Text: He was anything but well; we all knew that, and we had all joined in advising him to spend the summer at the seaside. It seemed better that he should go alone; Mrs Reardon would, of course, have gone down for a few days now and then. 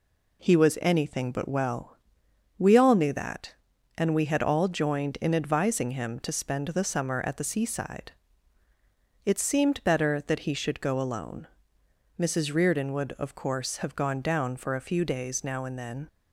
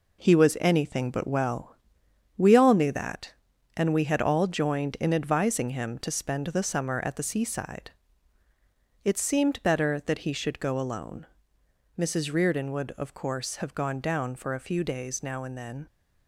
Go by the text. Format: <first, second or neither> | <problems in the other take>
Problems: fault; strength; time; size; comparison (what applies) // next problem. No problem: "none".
first | gets quieter; throughout; 6.5 dB